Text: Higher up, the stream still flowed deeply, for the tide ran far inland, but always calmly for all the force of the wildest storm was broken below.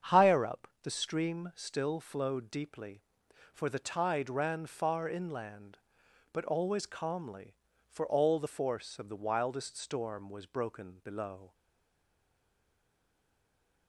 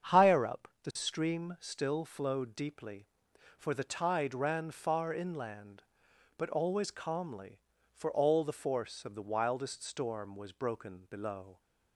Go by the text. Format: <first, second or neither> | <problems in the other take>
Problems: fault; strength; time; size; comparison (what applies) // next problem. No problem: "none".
second | starts louder than the rest; strong; until 1.2 s; 7.5 dB; strong in the second // stays silent after the last word; from 11.5 s on; 2.3 s long